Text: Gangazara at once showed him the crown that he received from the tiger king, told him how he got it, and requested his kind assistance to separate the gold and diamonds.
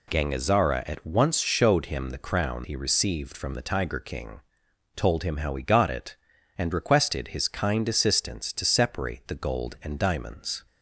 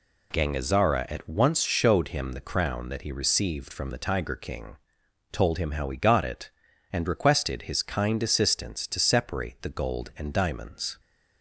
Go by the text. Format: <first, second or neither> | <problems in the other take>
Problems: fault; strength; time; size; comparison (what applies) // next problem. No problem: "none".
second | skips "that"; at 2.6 s